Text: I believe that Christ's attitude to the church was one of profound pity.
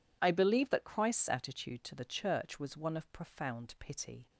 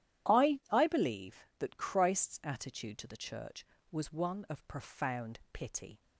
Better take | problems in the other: first | says "I" twice; at 0.7 s

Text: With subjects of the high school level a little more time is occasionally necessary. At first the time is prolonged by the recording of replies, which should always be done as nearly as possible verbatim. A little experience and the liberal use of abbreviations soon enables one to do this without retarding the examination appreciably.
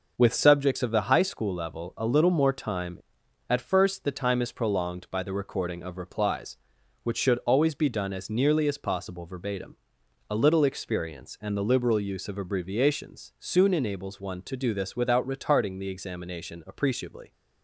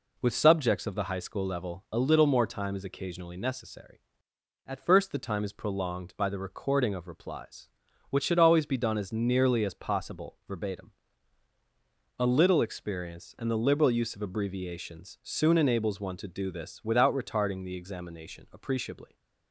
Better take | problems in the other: second | skips "is occasionally necessary"; at 3.2 s

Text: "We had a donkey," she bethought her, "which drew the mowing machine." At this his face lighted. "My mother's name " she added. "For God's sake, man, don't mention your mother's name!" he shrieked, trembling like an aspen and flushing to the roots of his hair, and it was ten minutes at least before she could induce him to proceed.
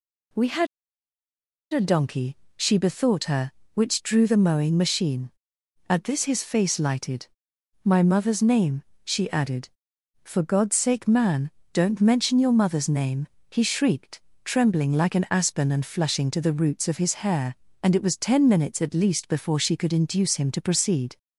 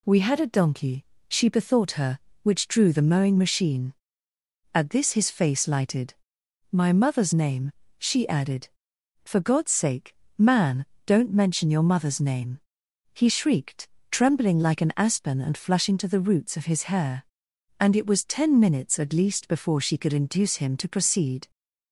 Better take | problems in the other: second | pauses between "had" and "a"; at 0.6 s; 1.0 s long

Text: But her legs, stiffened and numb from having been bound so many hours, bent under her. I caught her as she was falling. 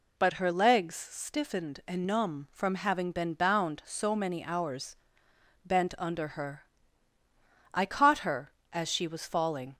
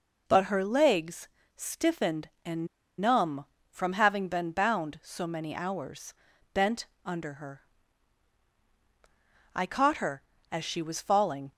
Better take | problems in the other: first | pauses between "and" and "numb"; slight; at 2.6 s; 0.32 s long // pauses between "bent" and "under"; slight; at 6.8 s; 0.18 s long

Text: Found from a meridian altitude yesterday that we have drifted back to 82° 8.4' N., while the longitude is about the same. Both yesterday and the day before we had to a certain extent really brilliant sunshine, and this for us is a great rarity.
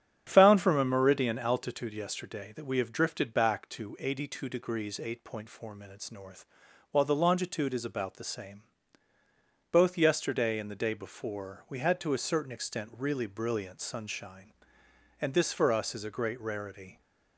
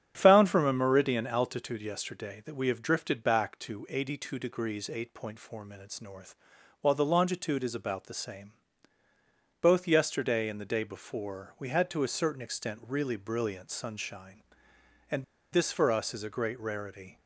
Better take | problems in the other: first | starts louder than the rest; strong; until 1.1 s; 9 dB; strong in the first // pauses between "and" and "this"; slight; at 15.2 s; 0.29 s long

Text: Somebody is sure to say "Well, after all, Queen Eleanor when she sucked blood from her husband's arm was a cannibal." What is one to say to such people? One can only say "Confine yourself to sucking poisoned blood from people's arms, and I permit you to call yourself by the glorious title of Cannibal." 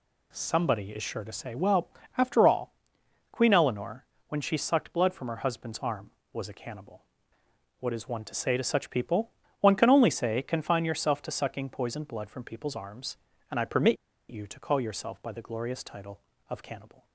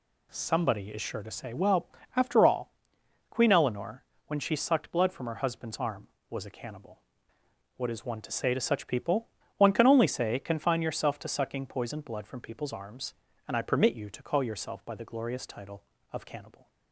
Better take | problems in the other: second | pauses between "Eleanor" and "when"; slight; at 4.0 s; 0.24 s long; slight in the second // pauses between "permit" and "you"; slight; at 13.9 s; 0.33 s long

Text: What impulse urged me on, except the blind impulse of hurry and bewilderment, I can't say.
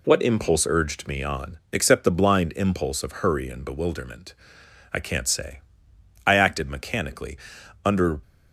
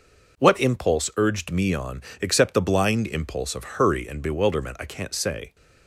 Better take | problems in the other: second | goes on to say "I acted mechanically under"; strong; from 6.2 s on; 1.9 s long

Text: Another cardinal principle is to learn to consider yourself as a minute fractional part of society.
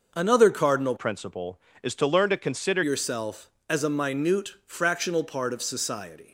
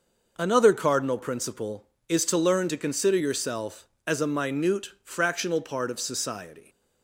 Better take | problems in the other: second | changes voice from "principle" to "consider"; from 0.9 to 2.8 s; 1.9 s long // pauses between "minute" and "fractional"; slight; at 4.4 s; 0.16 s long; slight in the second

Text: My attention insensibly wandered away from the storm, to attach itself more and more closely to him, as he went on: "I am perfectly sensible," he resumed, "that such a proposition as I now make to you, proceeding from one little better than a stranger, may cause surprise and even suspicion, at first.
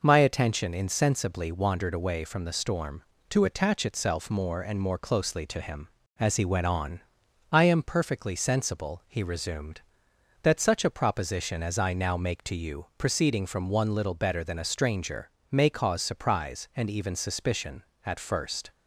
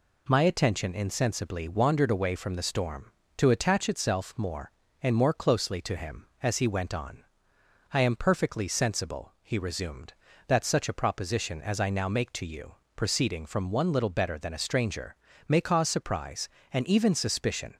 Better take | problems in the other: first | stops before "at first"; at 17.7 s

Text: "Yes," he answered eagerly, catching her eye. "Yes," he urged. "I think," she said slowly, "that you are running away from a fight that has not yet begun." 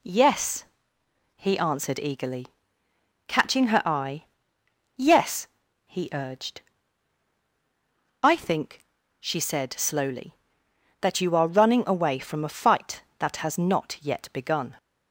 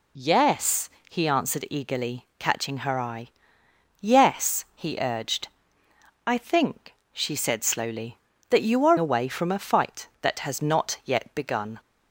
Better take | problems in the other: first | skips "running"; at 8.9 s

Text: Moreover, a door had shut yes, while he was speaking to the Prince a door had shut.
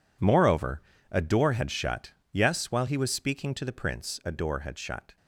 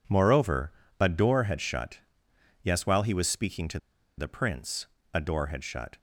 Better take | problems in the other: first | pauses between "shut" and "yes"; noticeable; at 1.9 s; 0.62 s long; slight in the first // pauses between "to" and "the"; at 3.7 s; 0.40 s long // pauses between "Prince" and "a"; slight; at 4.8 s; 0.30 s long

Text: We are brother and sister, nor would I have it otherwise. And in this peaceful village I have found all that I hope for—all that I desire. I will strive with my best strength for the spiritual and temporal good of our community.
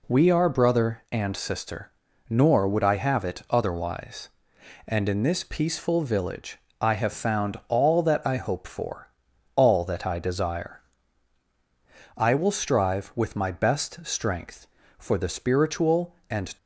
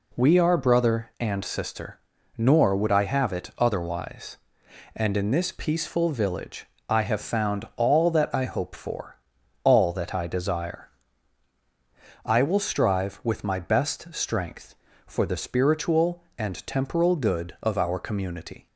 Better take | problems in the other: second | pauses between "village" and "I"; slight; at 6.5 s; 0.20 s long; slight in the second // stops before "temporal good of our community"; at 16.5 s

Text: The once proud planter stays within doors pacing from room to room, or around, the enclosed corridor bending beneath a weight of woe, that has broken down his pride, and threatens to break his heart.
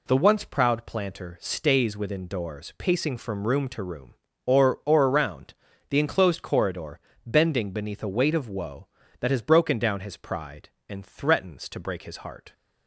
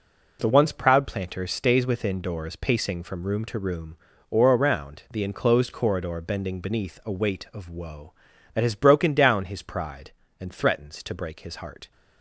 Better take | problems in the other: second | says "or" twice; at 4.8 s // pauses between "corridor" and "bending"; slight; at 7.0 s; 0.24 s long

